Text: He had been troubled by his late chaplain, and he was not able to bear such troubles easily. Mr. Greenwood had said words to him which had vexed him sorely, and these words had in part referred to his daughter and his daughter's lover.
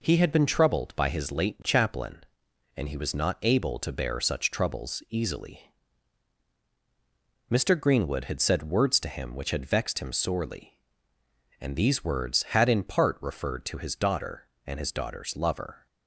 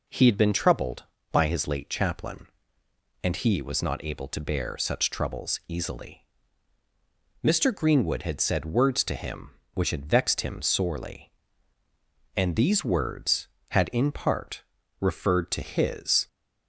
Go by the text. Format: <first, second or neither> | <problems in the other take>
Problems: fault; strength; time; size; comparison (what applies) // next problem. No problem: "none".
first | pauses between "part" and "referred"; slight; at 14.6 s; 0.36 s long // stops before "daughter and his daughter's lover"; at 16.2 s